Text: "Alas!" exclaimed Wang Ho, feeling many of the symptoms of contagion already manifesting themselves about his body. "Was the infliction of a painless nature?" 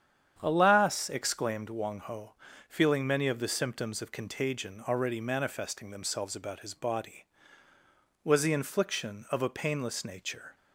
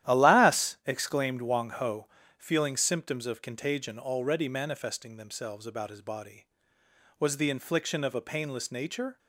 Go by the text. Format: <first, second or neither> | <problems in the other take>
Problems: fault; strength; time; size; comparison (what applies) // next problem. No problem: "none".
first | starts louder than the rest; strong; until 1.1 s; 12 dB; strong in the first // skips "many of the"; at 2.7 s